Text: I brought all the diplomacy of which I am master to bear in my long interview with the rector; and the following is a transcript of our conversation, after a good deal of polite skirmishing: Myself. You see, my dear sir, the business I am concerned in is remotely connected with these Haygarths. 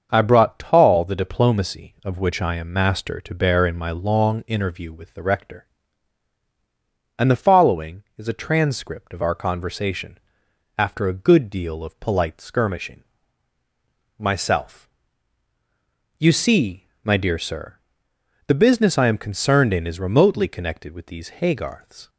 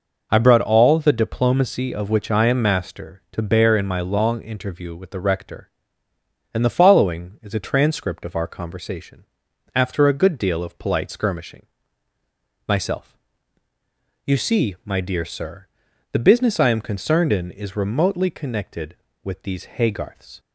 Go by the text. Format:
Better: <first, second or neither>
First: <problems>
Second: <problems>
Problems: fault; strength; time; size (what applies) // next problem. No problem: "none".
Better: second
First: starts louder than the rest; until 1.1 s; 6.5 dB // says "tall" for "all"; at 0.5 s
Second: none